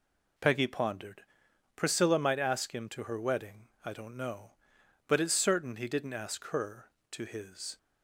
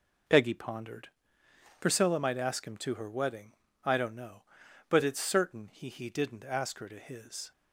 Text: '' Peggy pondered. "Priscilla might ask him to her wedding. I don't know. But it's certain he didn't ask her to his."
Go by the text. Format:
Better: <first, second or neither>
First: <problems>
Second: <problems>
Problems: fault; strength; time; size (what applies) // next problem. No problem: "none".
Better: first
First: none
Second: says "he" twice; at 5.8 s